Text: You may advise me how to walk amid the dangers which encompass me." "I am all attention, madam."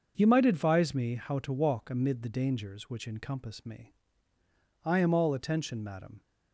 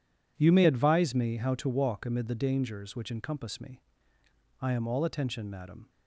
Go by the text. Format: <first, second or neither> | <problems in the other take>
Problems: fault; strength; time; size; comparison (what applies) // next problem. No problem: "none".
second | starts louder than the rest; until 1.1 s; 6 dB // says "might" for "may"; at 0.2 s